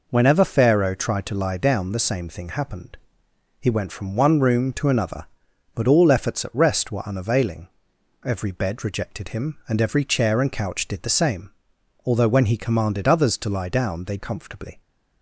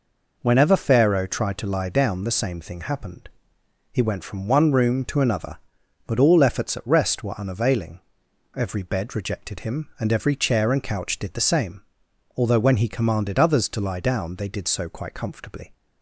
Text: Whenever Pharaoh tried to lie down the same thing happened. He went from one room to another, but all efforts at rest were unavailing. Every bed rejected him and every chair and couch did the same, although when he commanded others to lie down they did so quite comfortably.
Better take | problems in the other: second | skips "did so quite"; at 14.1 s

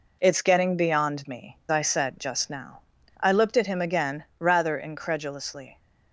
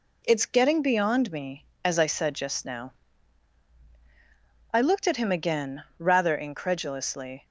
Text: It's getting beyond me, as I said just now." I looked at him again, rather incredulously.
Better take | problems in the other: second | skips "as"; at 1.6 s

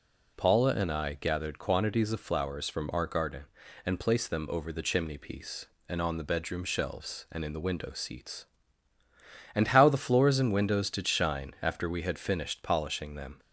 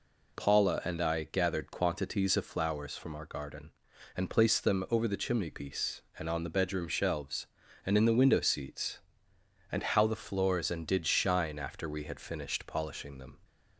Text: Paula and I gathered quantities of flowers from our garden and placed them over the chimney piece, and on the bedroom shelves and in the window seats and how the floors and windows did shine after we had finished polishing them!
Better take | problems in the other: first | skips "windows"; at 10.8 s

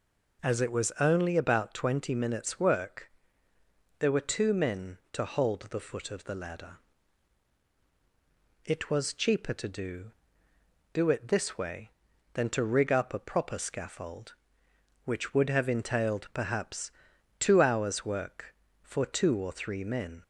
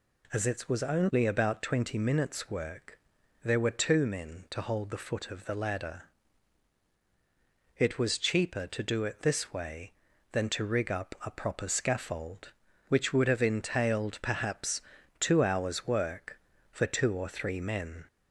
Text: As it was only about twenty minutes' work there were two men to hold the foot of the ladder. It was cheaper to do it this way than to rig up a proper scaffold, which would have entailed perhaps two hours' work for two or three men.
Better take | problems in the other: second | pauses between "work" and "there"; noticeable; at 3.1 s; 0.88 s long; noticeable in the second // says "do" twice; at 10.9 s // pauses between "perhaps" and "two"; noticeable; at 16.9 s; 0.48 s long; also in the second

